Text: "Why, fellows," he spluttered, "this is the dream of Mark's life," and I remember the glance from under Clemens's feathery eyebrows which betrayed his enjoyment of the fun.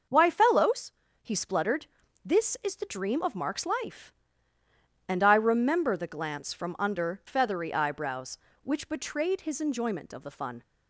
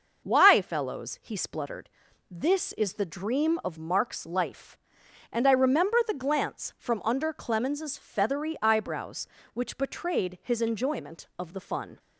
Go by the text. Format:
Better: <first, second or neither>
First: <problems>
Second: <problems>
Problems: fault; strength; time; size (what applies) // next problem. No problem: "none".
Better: second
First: starts louder than the rest; noticeable; until 1.4 s; 6 dB // skips "Clemens's"; at 7.2 s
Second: none